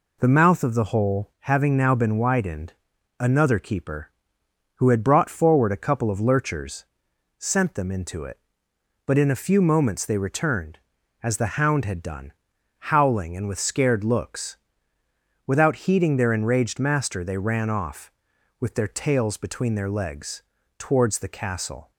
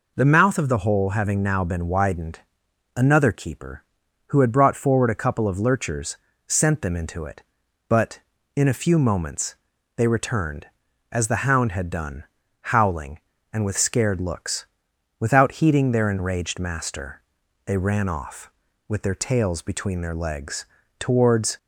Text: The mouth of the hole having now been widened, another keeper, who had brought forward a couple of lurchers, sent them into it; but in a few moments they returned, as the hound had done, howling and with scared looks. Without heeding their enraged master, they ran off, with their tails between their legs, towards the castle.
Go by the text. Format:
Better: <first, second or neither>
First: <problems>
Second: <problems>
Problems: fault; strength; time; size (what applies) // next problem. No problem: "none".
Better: first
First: none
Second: pauses between "moments" and "they"; at 9.5 s; 0.40 s long // stops before "the castle"; at 21.5 s